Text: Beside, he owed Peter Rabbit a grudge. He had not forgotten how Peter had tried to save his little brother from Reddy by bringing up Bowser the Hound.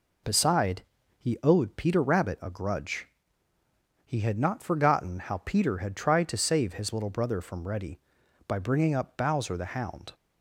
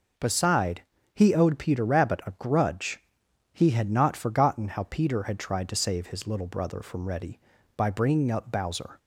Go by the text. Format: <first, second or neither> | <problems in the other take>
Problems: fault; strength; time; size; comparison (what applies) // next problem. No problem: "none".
first | stops before "the Hound"; at 8.9 s